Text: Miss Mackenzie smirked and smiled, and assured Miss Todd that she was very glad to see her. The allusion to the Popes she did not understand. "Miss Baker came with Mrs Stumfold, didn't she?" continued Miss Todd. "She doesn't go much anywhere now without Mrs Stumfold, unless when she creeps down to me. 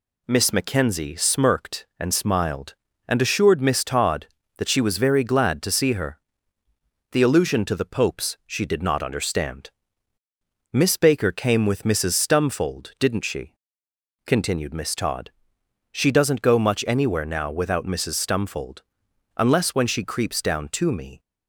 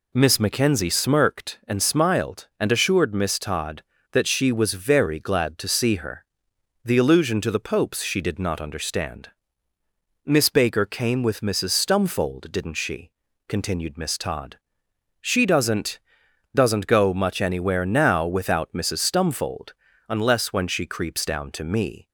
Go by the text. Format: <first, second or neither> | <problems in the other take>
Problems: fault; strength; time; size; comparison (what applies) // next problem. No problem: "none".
first | says "doesn't" twice; at 16.5 s